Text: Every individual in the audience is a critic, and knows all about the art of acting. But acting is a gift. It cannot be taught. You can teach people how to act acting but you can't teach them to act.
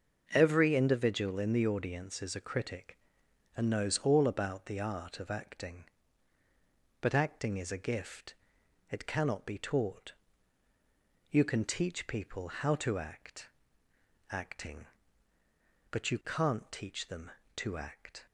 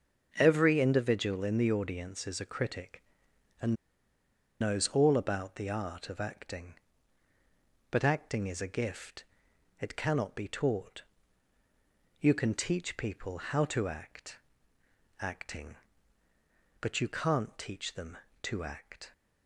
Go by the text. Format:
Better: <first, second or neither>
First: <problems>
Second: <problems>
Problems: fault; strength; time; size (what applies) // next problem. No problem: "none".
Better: first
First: starts louder than the rest; until 1.3 s; 6.5 dB // pauses between "act" and "acting"; noticeable; at 13.4 s; 0.80 s long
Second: starts louder than the rest; until 1.4 s; 6.5 dB // pauses between "and" and "knows"; noticeable; at 3.7 s; 0.85 s long // pauses between "act" and "acting"; noticeable; at 14.3 s; 0.80 s long